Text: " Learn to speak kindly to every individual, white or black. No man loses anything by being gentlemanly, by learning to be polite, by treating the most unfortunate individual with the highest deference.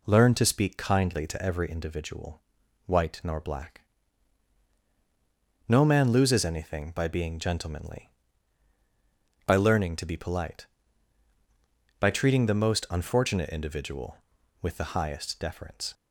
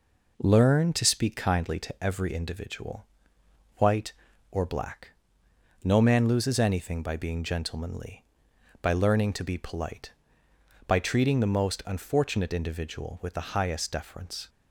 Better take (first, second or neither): second